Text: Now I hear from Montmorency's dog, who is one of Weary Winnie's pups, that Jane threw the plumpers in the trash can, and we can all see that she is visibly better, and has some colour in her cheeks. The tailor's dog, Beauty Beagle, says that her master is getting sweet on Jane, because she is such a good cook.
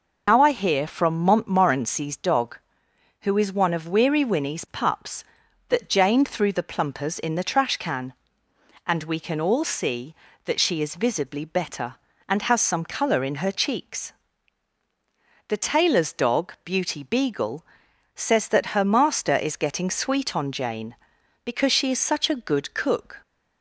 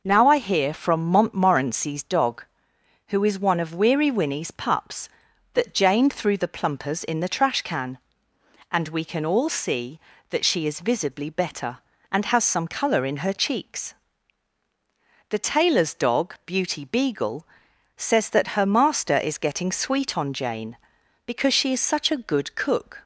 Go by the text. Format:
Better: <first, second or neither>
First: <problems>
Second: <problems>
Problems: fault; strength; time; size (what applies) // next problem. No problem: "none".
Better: second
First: loses the start of "Now"; at 0.2 s; 100 ms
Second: none